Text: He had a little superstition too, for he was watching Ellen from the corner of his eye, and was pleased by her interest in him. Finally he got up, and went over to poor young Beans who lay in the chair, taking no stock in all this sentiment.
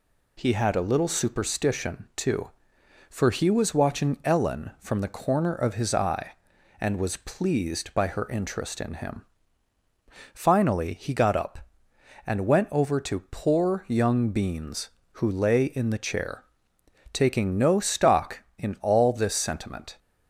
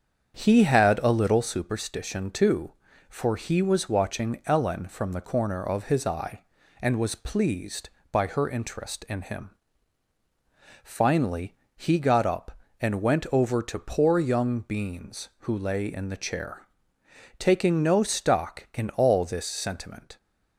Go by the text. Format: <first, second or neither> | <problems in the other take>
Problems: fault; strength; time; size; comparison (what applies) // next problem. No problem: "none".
first | starts louder than the rest; strong; until 1.5 s; 8 dB // pauses between "Finally" and "he"; slight; at 11.5 s; 0.22 s long